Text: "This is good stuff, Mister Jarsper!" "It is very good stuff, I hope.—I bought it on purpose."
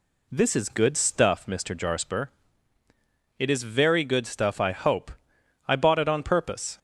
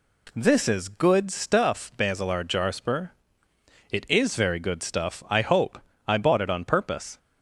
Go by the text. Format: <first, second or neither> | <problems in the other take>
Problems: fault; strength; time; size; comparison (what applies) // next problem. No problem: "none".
first | says "Basilar" for "Mister"; at 1.9 s